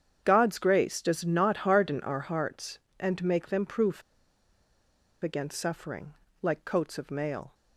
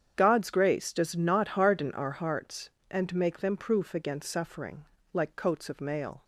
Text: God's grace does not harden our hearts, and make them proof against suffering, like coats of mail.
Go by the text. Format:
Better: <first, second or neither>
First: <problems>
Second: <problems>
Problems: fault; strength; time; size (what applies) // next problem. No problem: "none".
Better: second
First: starts louder than the rest; strong; until 1.2 s; 8 dB // pauses between "proof" and "against"; at 4.0 s; 1.2 s long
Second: starts louder than the rest; strong; until 1.2 s; 8 dB